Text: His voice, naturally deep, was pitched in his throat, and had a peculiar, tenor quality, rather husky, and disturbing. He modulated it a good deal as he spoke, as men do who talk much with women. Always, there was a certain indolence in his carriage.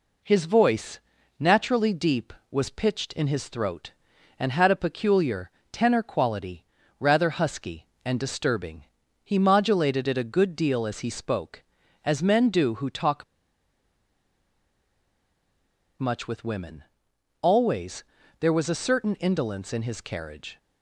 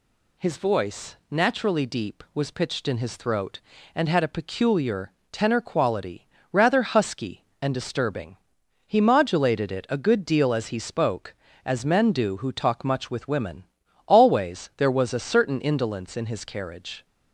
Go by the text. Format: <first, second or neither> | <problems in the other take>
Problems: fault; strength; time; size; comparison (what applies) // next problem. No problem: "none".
second | pauses between "talk" and "much"; strong; at 13.2 s; 2.7 s long